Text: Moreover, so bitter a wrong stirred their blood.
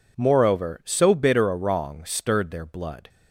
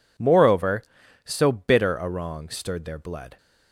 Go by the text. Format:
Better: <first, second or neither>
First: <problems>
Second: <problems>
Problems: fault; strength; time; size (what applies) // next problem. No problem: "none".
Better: neither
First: none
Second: none